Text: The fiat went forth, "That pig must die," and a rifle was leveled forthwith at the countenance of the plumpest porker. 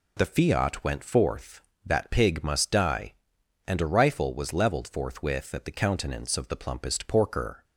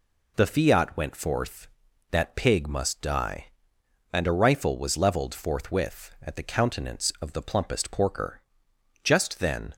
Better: first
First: none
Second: goes on to say "Just then"; noticeable; from 9.0 s on; 0.70 s long

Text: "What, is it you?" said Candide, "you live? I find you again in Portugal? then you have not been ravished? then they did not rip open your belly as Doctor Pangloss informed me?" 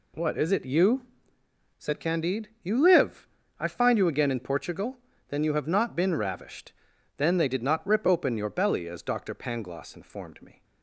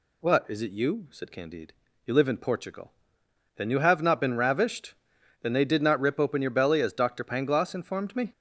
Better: first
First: none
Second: skips "I find you again"; at 2.2 s

